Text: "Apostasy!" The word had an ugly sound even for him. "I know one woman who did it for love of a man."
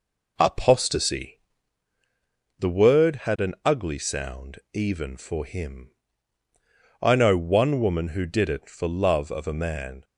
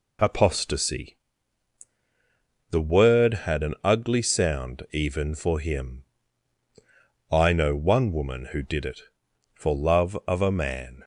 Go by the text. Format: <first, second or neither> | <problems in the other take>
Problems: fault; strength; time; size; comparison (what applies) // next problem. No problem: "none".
second | starts louder than the rest; noticeable; until 1.8 s; 4 dB